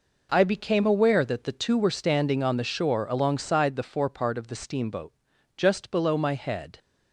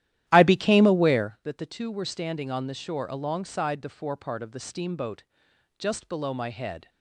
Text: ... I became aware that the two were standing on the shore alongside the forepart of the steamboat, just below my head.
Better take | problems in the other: first | starts louder than the rest; strong; until 1.4 s; 13 dB

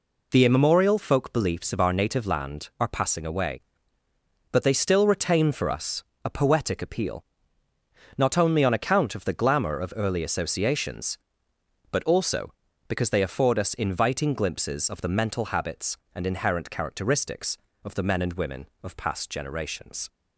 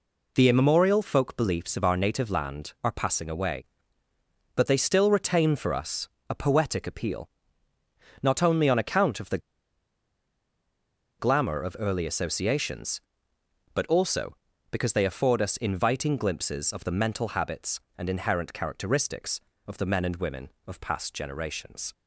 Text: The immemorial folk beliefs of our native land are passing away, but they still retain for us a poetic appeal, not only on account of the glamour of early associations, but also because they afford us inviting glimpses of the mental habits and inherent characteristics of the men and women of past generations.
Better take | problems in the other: first | pauses between "us" and "a"; slight; at 6.0 s; 0.20 s long; slight in the first // pauses between "the" and "glamour"; strong; at 9.3 s; 1.8 s long

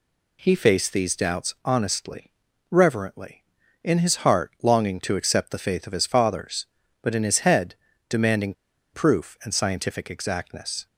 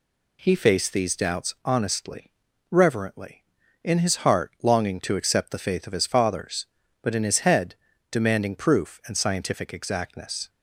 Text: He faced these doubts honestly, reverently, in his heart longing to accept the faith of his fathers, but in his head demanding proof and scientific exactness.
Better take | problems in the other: second | pauses between "head" and "demanding"; slight; at 7.7 s; 0.34 s long; slight in the second // pauses between "demanding" and "proof"; at 8.5 s; 0.39 s long

